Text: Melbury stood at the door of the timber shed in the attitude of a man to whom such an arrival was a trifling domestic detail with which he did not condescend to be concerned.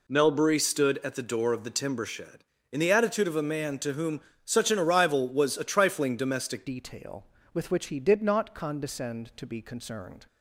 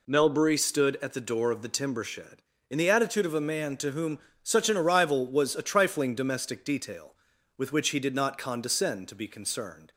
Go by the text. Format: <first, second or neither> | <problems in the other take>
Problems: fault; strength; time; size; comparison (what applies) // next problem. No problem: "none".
second | pauses between "whom" and "such"; slight; at 4.2 s; 0.24 s long; slight in the second // changes voice at "detail"; from 6.6 s on; 3.6 s long